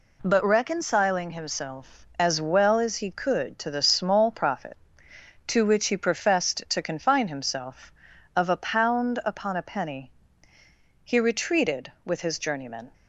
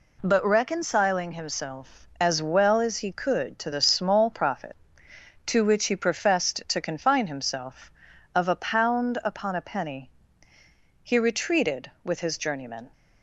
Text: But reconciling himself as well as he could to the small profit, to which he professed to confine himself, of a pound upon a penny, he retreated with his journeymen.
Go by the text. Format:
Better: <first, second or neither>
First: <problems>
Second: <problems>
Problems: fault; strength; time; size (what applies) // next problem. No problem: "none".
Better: neither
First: none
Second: none